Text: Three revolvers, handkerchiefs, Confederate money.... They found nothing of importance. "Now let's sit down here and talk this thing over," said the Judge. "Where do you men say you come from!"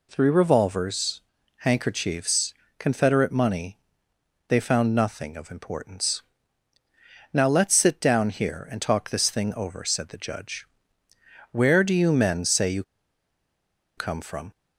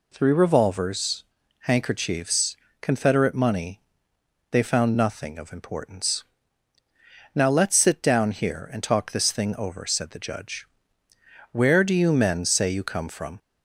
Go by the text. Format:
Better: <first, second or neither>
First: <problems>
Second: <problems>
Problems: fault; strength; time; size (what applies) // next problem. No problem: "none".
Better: second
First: pauses between "you" and "come"; at 12.8 s; 1.1 s long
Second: none